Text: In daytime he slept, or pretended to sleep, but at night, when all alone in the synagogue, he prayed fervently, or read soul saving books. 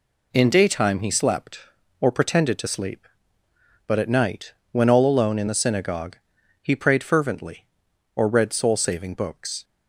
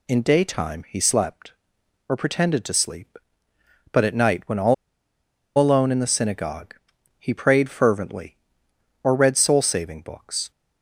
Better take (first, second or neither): first